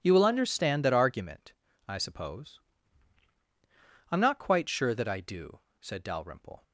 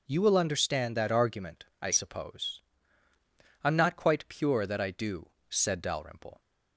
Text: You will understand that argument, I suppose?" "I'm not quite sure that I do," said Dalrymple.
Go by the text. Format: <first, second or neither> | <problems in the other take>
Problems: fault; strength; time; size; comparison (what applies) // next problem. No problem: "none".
first | says "pure" for "sure"; at 4.2 s